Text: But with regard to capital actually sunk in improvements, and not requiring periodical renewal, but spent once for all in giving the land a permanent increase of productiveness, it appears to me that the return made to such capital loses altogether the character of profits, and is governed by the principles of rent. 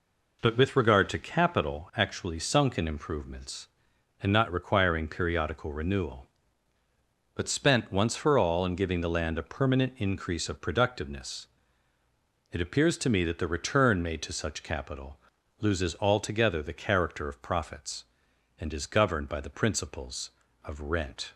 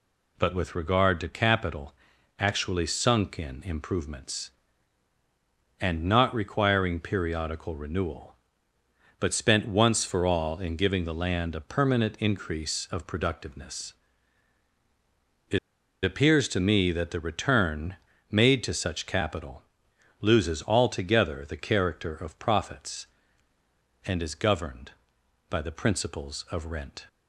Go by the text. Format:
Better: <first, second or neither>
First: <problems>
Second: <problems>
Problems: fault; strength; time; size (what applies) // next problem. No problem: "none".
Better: first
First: pauses between "capital" and "loses"; at 15.1 s; 0.42 s long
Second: pauses between "capital" and "actually"; noticeable; at 1.9 s; 0.46 s long // pauses between "it" and "appears"; at 15.5 s; 0.44 s long // pauses between "return" and "made"; slight; at 17.9 s; 0.34 s long // pauses between "capital" and "loses"; noticeable; at 19.6 s; 0.56 s long